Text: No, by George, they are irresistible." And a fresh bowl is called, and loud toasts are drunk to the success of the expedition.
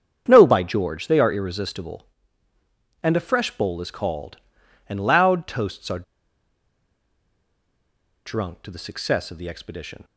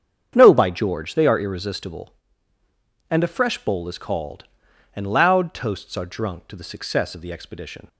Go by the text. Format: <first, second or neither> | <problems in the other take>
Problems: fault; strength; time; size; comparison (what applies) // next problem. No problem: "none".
second | starts louder than the rest; strong; until 1.3 s; 7.5 dB; strong in the second // pauses between "are" and "drunk"; strong; at 6.0 s; 2.2 s long